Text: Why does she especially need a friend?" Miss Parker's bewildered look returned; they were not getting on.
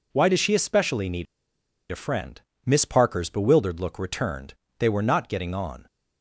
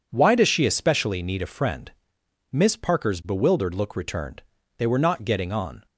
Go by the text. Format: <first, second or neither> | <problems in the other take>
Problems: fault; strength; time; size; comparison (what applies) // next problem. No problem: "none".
second | pauses between "need" and "a"; noticeable; at 1.2 s; 0.67 s long